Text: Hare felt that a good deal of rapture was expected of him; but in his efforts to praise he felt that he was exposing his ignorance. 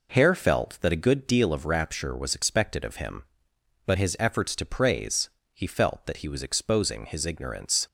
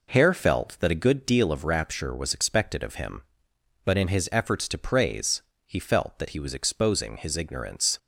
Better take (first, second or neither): second